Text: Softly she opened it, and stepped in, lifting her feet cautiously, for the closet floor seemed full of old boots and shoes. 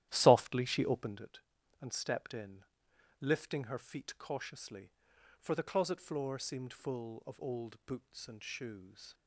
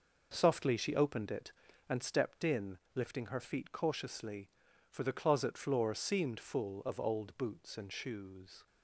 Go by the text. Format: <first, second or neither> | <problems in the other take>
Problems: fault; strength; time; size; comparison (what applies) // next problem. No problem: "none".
second | starts louder than the rest; strong; until 1.2 s; 12.5 dB